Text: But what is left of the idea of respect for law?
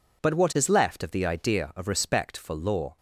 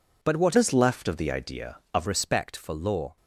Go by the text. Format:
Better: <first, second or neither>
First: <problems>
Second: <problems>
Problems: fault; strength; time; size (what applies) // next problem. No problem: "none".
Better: first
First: none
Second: changes voice from "is" to "of"; from 0.5 to 2.0 s; 1.5 s long